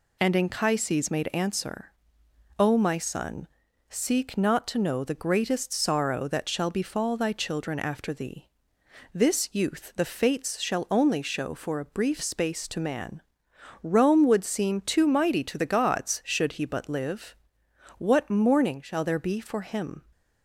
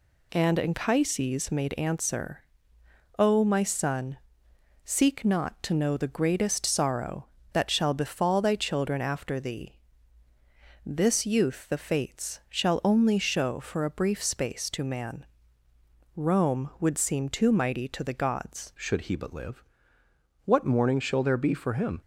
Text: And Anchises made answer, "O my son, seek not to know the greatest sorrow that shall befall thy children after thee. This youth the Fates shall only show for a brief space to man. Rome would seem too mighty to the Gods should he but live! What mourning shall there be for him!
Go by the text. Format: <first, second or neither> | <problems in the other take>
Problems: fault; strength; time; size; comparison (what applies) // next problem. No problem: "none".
first | changes voice at "should"; from 18.7 s on; 3.3 s long